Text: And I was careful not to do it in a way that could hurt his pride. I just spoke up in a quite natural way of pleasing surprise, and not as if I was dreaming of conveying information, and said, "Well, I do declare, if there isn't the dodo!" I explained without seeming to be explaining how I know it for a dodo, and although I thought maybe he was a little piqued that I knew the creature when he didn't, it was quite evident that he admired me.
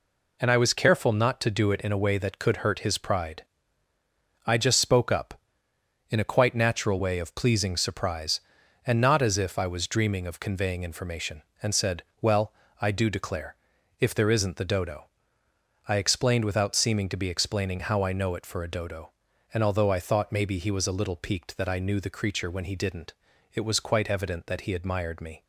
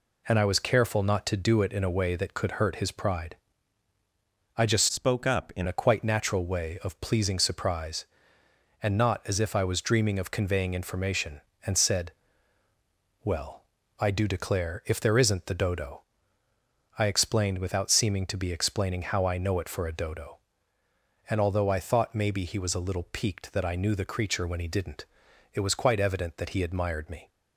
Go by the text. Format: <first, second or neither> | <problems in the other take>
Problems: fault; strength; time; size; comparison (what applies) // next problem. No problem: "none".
first | changes voice from "spoke" to "in"; from 4.9 to 5.6 s; 0.7 s long